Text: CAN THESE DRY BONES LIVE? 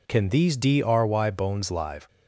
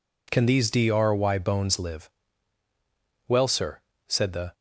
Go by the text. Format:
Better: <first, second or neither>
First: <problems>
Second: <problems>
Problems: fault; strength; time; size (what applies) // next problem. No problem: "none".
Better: first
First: none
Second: goes on to say "Well sir said the"; noticeable; from 3.2 s on; 1.2 s long